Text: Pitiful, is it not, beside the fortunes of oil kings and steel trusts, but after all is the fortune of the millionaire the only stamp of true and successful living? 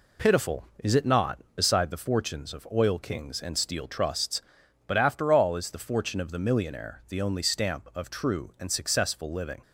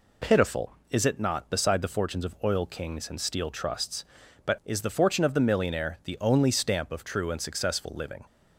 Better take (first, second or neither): first